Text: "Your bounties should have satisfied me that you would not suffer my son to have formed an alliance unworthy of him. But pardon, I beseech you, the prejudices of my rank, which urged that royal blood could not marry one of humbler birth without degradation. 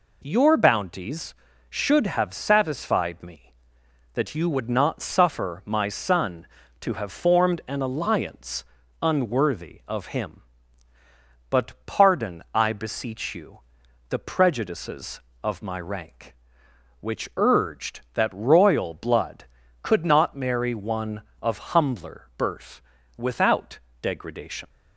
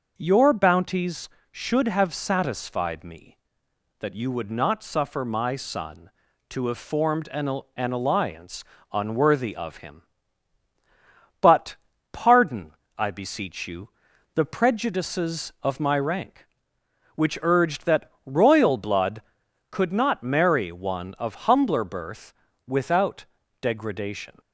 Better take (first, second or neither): first